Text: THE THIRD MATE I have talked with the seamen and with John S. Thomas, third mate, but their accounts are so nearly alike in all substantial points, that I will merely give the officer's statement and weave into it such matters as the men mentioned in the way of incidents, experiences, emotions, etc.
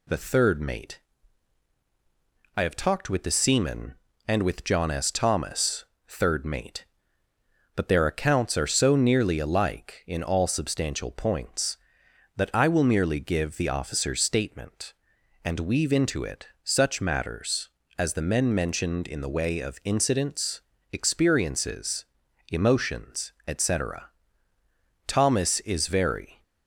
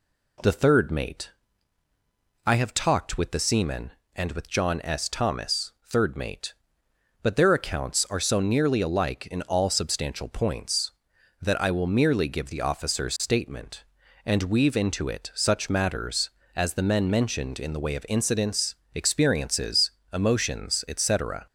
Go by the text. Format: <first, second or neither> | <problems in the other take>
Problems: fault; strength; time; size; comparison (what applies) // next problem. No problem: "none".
second | pauses between "MATE" and "I"; strong; at 1.0 s; 1.5 s long; also in the second // pauses between "it" and "such"; slight; at 16.4 s; 0.16 s long // goes on to say "Thomas is very"; from 25.0 s on; 1.3 s long